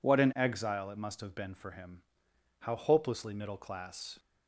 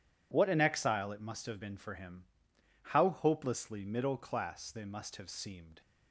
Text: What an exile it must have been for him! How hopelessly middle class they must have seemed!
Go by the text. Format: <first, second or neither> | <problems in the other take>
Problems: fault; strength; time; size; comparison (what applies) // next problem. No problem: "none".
second | stops before "they must have seemed"; at 4.1 s